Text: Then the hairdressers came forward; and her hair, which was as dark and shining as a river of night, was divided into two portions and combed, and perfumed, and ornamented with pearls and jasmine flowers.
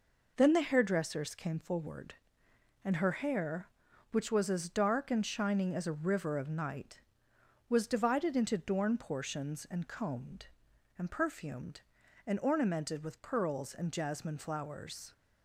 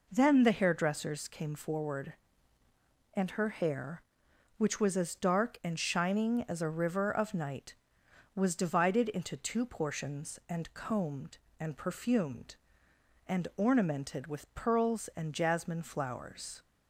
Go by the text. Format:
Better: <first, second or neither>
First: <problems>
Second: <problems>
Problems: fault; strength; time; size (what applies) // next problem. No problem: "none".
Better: second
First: says "dorn" for "two"; at 8.5 s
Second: none